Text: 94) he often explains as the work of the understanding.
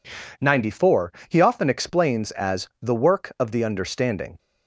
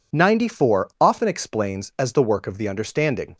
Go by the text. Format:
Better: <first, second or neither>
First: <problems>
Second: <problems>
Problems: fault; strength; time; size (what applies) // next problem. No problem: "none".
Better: first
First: none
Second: skips "he"; at 0.9 s